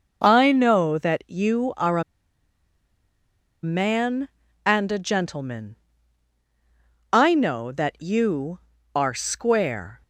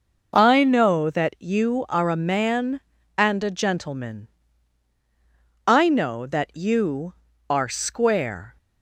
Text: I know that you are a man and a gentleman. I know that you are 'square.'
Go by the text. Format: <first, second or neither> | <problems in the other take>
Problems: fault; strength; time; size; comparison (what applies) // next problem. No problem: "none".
second | pauses between "a" and "man"; strong; at 2.0 s; 1.6 s long